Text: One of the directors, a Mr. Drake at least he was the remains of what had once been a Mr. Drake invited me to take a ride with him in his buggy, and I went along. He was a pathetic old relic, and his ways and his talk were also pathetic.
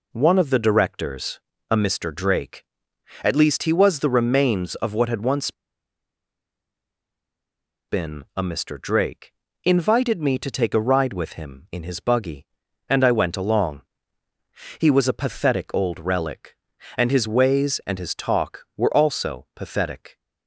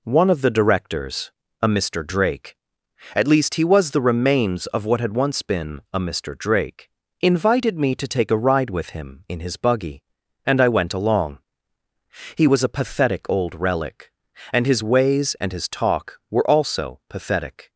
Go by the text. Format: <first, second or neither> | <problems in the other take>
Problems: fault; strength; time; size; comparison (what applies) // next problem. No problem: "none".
second | pauses between "once" and "been"; strong; at 5.5 s; 2.3 s long // pauses between "Drake" and "invited"; slight; at 9.3 s; 0.32 s long; slight in the second